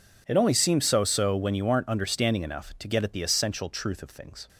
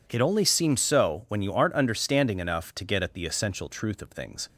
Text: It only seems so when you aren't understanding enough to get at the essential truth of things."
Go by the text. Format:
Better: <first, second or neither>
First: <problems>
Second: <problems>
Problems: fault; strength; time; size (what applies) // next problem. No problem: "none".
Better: second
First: says "so" twice; at 1.0 s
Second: none